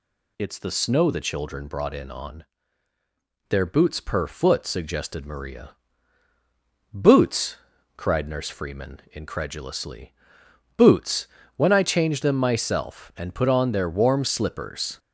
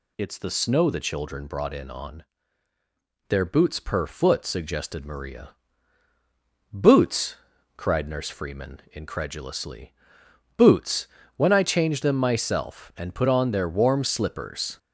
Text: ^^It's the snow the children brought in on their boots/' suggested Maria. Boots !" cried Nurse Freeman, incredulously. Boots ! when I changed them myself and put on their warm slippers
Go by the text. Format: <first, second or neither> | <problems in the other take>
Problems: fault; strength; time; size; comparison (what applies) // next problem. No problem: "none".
neither | pauses between "on" and "their"; the same in both